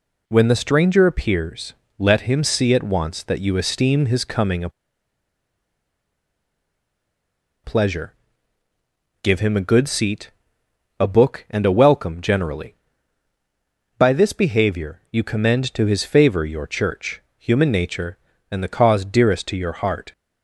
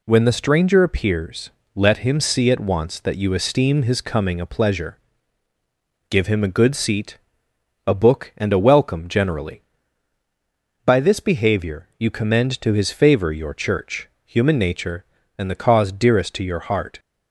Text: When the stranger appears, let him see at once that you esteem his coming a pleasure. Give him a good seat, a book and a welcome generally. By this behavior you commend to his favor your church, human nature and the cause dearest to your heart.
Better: second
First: pauses between "a" and "pleasure"; strong; at 4.6 s; 2.9 s long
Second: none

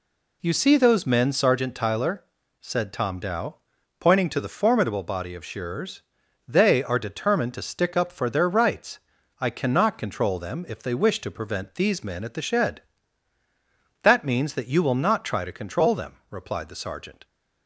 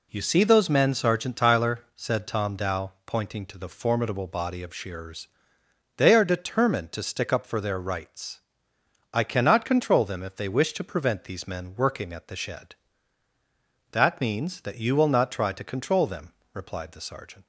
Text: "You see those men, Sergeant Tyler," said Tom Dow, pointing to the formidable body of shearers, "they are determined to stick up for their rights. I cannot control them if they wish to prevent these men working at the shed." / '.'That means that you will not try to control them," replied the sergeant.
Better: second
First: skips "working"; at 12.2 s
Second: none

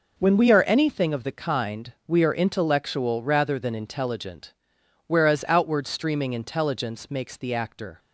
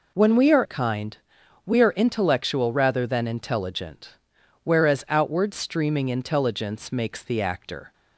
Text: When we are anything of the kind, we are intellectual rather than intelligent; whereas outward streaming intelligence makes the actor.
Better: first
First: none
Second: skips "anything of the"; at 0.6 s

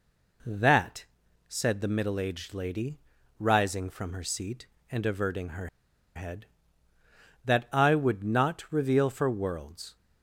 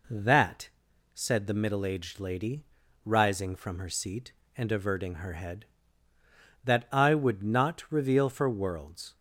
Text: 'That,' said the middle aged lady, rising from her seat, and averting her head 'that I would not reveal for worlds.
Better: second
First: pauses between "her" and "head"; noticeable; at 5.6 s; 0.48 s long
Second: none

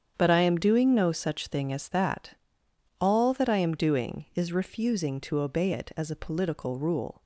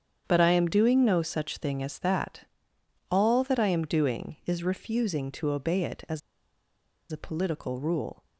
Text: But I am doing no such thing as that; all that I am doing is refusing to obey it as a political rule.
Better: first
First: starts louder than the rest; strong; until 1.1 s; 8 dB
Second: starts louder than the rest; strong; until 1.2 s; 8 dB // pauses between "as" and "a"; noticeable; at 6.2 s; 0.91 s long

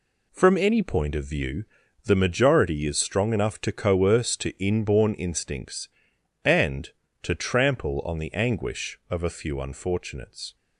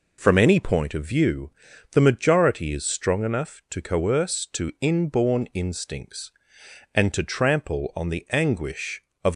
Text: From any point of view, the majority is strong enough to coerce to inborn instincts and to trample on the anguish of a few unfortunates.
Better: first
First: none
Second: stops before "a few unfortunates"; at 9.3 s

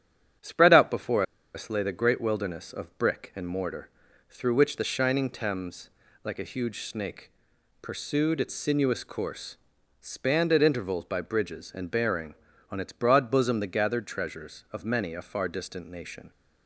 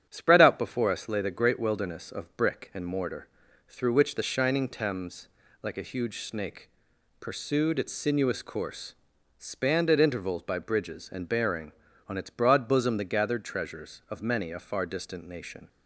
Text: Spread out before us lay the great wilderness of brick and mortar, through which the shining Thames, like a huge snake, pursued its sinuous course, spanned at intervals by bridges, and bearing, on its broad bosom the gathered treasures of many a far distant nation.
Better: second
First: starts louder than the rest; strong; until 1.7 s; 9.5 dB // pauses between "before" and "us"; slight; at 1.2 s; 0.31 s long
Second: starts louder than the rest; strong; until 1.1 s; 9.5 dB

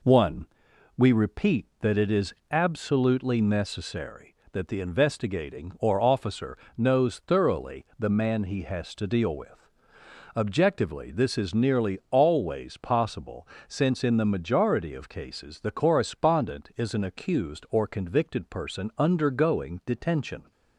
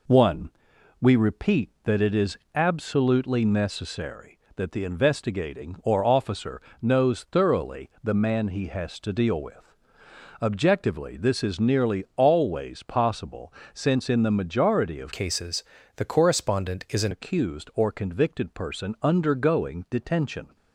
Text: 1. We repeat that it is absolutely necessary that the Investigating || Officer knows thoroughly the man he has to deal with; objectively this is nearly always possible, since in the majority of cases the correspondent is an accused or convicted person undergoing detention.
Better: first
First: pauses between "is" and "absolutely"; slight; at 2.3 s; 0.16 s long // pauses between "Officer" and "knows"; slight; at 6.5 s; 0.21 s long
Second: pauses between "is" and "absolutely"; slight; at 2.3 s; 0.16 s long // pauses between "Officer" and "knows"; slight; at 6.5 s; 0.22 s long // changes voice from "cases" to "an"; from 15.1 to 17.1 s; 2.0 s long // pauses between "cases" and "the"; slight; at 15.6 s; 0.32 s long

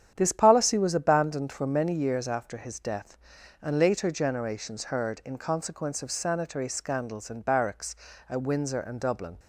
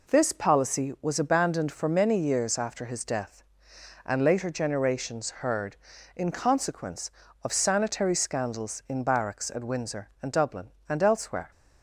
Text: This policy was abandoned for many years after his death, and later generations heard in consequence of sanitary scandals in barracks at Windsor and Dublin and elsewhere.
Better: second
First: starts louder than the rest; strong; until 1.1 s; 9 dB // stops before "and elsewhere"; at 9.3 s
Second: none

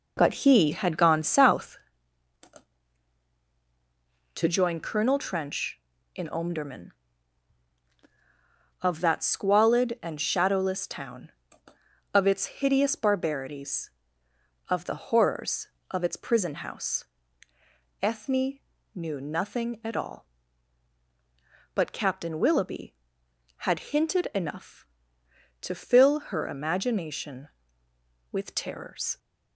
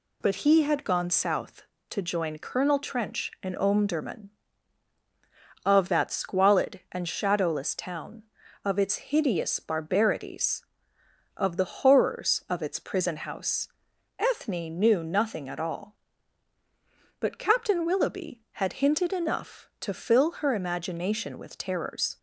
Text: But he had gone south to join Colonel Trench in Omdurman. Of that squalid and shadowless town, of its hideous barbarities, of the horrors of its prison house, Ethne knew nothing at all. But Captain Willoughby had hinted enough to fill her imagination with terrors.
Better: second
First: starts louder than the rest; noticeable; until 1.9 s; 4.5 dB // pauses between "Ethne" and "knew"; at 18.5 s; 0.38 s long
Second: none

